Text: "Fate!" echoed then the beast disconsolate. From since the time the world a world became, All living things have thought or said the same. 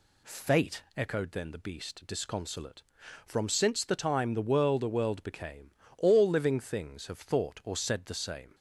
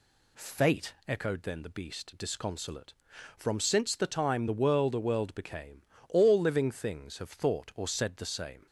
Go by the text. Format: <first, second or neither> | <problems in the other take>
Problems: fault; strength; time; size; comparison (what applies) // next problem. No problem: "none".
neither | none